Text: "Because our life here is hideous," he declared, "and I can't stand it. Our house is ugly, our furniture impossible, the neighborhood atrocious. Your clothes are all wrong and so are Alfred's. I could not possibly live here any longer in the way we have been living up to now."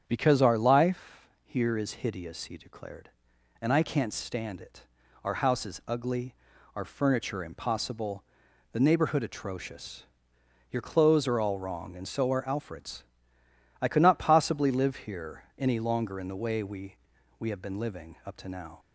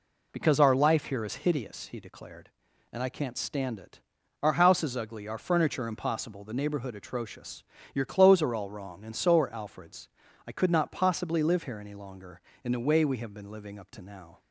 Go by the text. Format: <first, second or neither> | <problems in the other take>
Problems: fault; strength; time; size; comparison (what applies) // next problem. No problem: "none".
second | starts louder than the rest; strong; until 1.0 s; 8 dB // pauses between "life" and "here"; slight; at 1.2 s; 0.18 s long // says "we" twice; at 17.3 s